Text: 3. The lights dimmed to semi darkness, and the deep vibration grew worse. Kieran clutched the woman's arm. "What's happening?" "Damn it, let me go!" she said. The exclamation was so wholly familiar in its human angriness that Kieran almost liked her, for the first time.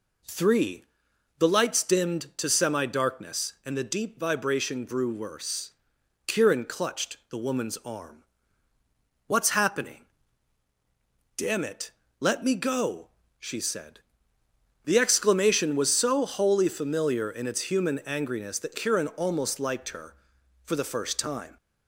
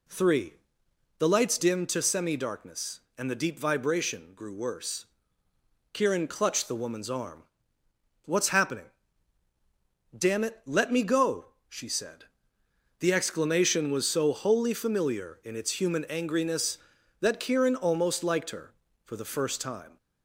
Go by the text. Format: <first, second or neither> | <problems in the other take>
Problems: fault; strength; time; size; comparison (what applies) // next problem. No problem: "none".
neither | none